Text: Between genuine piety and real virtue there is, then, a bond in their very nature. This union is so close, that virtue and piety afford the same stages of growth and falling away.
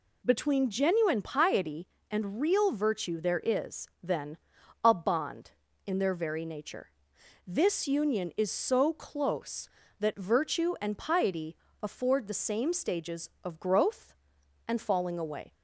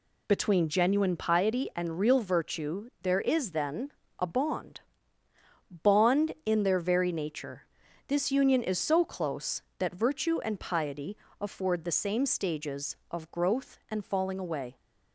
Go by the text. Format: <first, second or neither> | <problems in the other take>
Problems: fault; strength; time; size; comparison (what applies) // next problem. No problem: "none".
first | says "bond" twice; at 5.8 s // pauses between "piety" and "afford"; slight; at 11.1 s; 0.24 s long; slight in the first